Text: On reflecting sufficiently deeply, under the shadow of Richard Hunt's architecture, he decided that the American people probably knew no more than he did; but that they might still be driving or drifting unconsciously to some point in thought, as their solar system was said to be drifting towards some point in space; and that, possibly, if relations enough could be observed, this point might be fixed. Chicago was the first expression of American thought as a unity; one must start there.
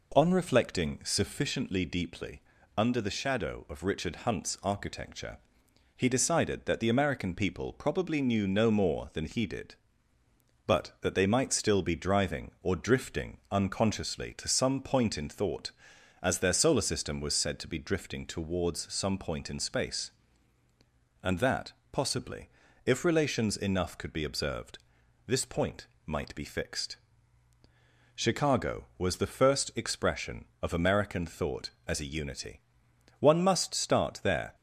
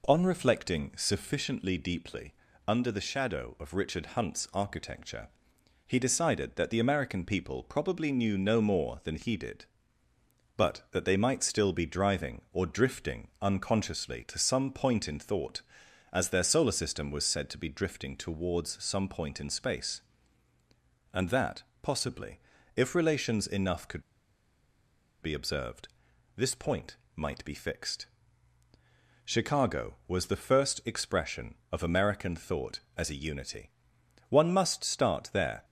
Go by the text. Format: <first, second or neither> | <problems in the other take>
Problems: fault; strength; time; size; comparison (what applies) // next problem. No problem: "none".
first | pauses between "could" and "be"; at 24.0 s; 1.1 s long // pauses between "point" and "might"; slight; at 26.9 s; 0.20 s long; slight in the first